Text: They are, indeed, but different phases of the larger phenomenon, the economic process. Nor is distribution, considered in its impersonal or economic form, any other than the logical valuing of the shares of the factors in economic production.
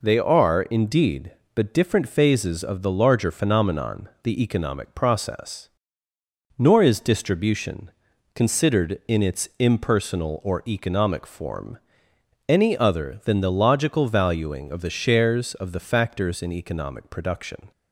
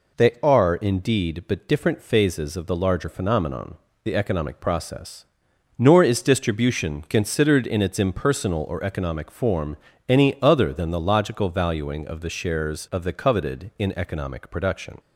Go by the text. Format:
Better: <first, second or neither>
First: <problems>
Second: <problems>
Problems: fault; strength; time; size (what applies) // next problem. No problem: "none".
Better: first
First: none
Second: says "coveted" for "factors"; at 13.1 s